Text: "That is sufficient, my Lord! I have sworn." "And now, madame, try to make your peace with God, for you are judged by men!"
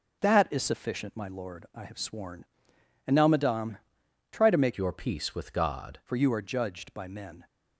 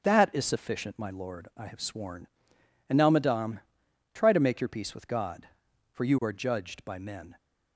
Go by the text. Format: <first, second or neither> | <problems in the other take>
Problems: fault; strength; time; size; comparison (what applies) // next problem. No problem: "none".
second | starts louder than the rest; until 1.2 s; 6 dB; also in the second // changes voice from "your" to "God"; from 4.7 to 5.9 s; 1.2 s long